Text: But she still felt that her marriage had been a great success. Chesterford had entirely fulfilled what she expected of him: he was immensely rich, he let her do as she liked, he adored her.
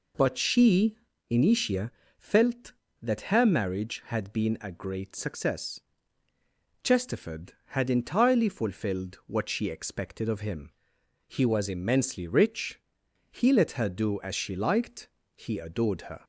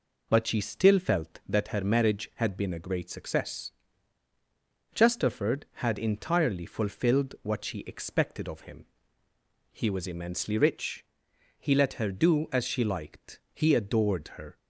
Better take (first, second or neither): second